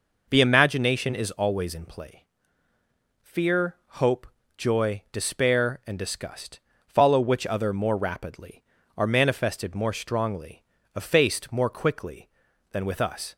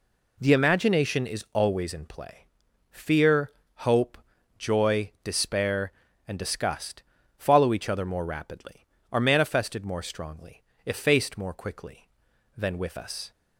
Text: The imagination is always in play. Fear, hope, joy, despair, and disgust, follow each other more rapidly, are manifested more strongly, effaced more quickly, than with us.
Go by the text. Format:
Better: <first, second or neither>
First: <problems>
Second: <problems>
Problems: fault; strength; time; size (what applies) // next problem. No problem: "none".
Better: second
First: says "which" for "each"; at 7.1 s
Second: none